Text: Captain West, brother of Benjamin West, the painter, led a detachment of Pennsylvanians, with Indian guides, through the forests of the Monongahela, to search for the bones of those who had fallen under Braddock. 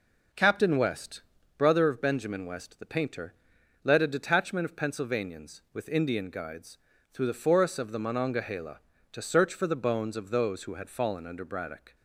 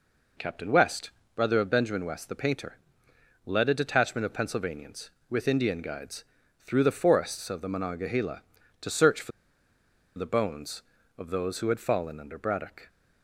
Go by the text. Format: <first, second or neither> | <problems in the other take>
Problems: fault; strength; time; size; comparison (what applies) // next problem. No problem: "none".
first | pauses between "for" and "the"; noticeable; at 9.3 s; 0.87 s long